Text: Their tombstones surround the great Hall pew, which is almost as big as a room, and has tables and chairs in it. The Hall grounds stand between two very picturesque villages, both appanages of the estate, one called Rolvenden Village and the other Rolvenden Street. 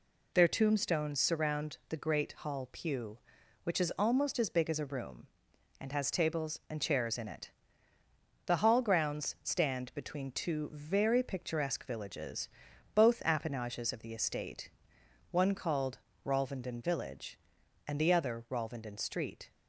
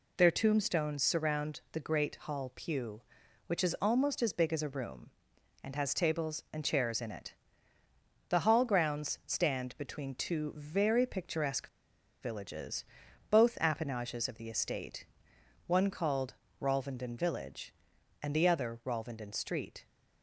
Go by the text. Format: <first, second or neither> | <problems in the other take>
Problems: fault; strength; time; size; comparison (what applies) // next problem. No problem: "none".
first | pauses between "picturesque" and "villages"; noticeable; at 11.6 s; 0.54 s long // pauses between "called" and "Rolvenden"; slight; at 16.3 s; 0.26 s long; slight in the first